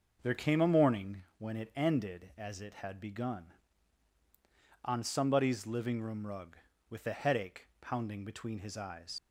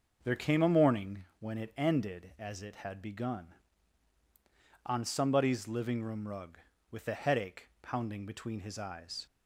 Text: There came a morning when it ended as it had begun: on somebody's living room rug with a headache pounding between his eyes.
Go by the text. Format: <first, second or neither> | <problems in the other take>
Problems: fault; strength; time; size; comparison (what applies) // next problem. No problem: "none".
second | starts louder than the rest; until 1.2 s; 6 dB; also in the second // pauses between "morning" and "when"; slight; at 1.2 s; 0.16 s long; slight in the second // leaves "eyes" unfinished; at 9.1 s; 60 ms